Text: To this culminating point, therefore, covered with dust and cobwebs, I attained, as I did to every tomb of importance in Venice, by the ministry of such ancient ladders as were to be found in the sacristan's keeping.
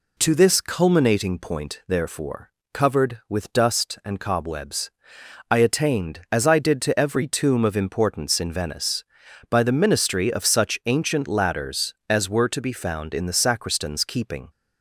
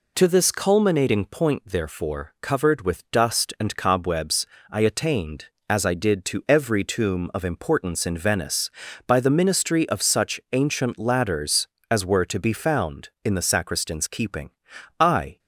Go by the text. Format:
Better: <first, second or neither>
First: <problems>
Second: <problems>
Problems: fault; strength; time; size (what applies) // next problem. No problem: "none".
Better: first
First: none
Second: goes on to say "I"; slight; from 15.0 s on; 0.38 s long